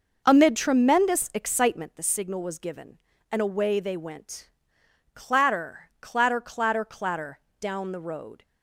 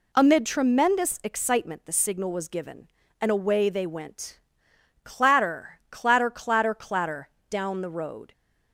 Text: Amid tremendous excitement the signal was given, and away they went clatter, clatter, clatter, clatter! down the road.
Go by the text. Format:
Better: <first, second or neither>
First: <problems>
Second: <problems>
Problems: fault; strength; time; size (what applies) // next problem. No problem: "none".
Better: second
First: starts louder than the rest; noticeable; until 2.1 s; 6 dB // pauses between "went" and "clatter"; noticeable; at 4.5 s; 0.64 s long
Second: pauses between "went" and "clatter"; noticeable; at 4.4 s; 0.64 s long